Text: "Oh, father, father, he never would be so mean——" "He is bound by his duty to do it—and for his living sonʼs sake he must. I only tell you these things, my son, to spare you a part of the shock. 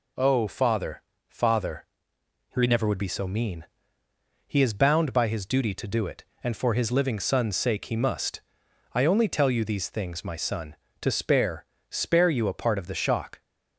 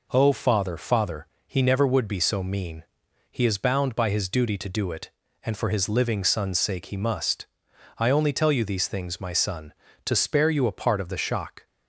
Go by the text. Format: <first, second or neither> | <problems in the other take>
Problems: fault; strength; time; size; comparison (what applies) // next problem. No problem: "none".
second | says "spare" twice; at 11.8 s